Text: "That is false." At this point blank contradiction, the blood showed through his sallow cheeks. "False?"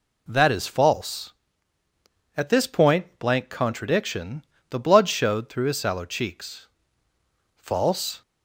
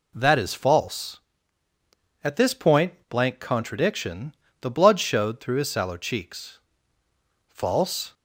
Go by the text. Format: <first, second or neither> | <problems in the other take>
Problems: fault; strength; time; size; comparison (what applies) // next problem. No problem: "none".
neither | none